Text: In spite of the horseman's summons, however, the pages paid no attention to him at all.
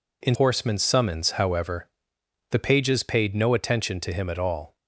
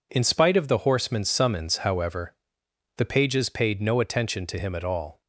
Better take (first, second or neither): second